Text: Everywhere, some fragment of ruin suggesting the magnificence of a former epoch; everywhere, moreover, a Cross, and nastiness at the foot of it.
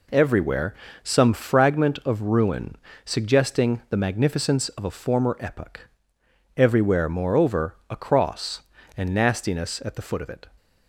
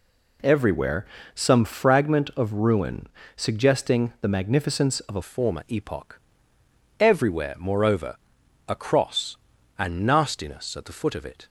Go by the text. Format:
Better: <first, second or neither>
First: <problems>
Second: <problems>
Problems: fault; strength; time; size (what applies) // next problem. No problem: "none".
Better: first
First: pauses between "ruin" and "suggesting"; slight; at 2.7 s; 0.30 s long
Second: pauses between "ruin" and "suggesting"; slight; at 3.0 s; 0.30 s long // changes voice at "former"; from 5.2 s on; 6.2 s long